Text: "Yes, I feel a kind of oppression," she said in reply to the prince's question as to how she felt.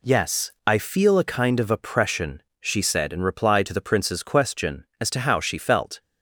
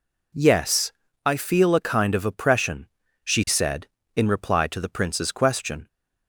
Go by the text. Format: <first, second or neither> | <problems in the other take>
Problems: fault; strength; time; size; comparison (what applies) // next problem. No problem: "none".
first | stops before "as to how she felt"; at 5.8 s